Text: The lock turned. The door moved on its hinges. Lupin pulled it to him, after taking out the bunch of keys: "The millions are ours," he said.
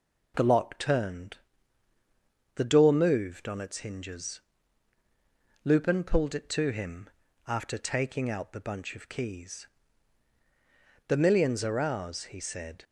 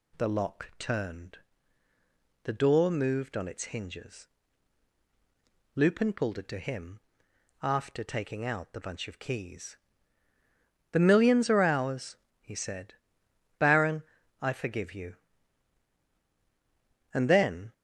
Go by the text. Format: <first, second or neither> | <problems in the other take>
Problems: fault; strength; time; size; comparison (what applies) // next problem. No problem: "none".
first | goes on to say "Baron I forgive you And then"; strong; from 13.5 s on; 4.1 s long